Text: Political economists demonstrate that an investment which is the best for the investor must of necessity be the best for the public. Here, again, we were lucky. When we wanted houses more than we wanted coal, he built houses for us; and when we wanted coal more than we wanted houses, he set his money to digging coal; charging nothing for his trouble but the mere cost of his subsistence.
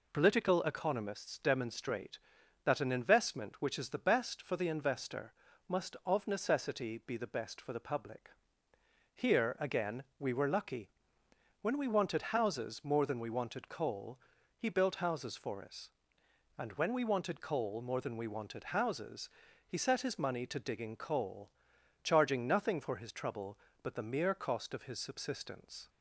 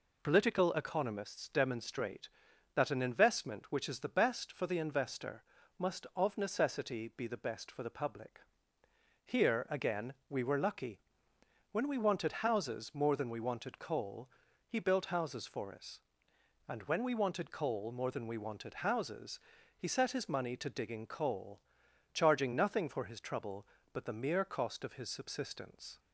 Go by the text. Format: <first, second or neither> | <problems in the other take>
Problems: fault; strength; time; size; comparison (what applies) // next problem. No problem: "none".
neither | pauses between "investor" and "must"; slight; the same in both